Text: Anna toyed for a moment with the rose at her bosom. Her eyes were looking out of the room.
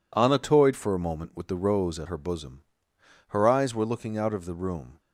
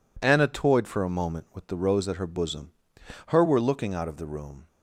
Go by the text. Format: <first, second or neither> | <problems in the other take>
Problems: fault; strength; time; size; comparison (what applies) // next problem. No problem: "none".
first | skips "eyes"; at 3.4 s